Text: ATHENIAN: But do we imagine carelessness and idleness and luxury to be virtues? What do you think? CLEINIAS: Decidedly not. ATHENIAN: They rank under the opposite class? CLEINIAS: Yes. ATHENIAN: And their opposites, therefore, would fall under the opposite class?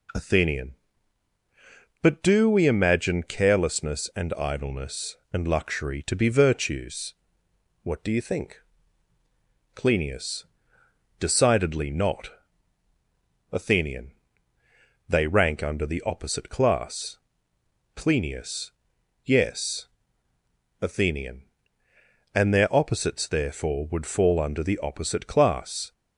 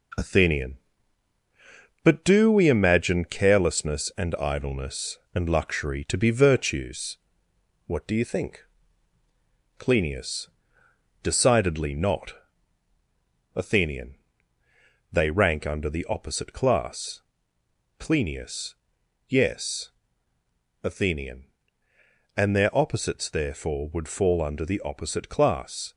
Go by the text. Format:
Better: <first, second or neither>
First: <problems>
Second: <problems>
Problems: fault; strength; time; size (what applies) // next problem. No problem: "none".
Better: first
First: none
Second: gets quieter; noticeable; throughout; 4.5 dB